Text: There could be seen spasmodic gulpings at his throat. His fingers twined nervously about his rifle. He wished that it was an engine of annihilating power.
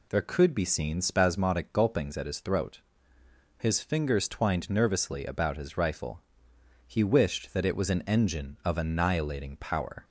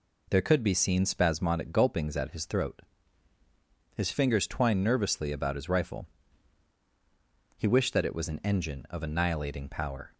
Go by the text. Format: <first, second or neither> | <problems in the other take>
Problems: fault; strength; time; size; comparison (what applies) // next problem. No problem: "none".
neither | none